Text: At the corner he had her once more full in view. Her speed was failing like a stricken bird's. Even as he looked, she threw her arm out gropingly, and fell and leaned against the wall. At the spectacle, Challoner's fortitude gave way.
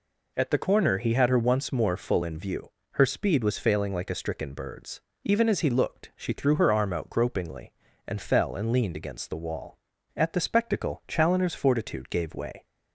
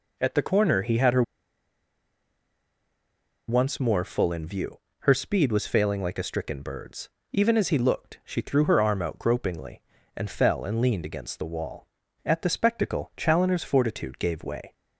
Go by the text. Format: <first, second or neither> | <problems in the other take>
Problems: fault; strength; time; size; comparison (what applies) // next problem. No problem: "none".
first | pauses between "her" and "once"; strong; at 1.2 s; 2.2 s long